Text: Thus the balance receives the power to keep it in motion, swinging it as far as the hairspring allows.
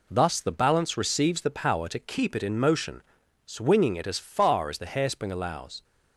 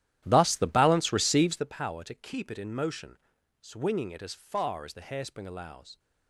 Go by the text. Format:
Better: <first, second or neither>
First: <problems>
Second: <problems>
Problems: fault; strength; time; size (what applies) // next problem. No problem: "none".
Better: first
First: none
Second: starts louder than the rest; strong; until 1.8 s; 12.5 dB